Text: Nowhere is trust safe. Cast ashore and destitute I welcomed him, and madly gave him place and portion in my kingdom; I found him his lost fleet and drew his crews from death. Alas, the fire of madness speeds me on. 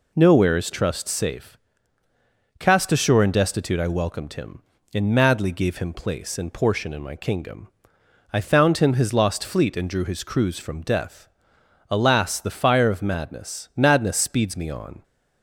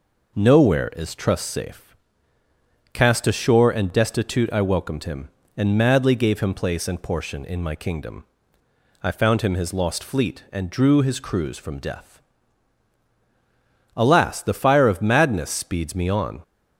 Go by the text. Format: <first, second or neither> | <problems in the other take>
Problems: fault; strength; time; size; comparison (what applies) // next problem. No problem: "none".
second | says "madness" twice; at 13.7 s